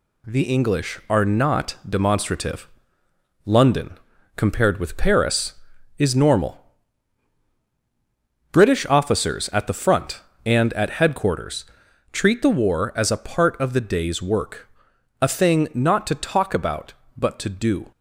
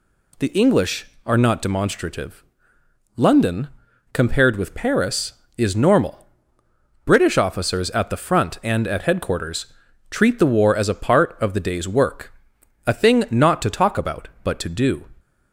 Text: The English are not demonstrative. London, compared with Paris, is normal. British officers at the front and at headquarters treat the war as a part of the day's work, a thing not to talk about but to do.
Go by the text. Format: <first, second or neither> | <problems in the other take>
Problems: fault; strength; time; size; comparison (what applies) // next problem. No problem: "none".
second | gets quieter; noticeable; throughout; 4.5 dB // pauses between "headquarters" and "treat"; noticeable; at 11.6 s; 0.46 s long; also in the second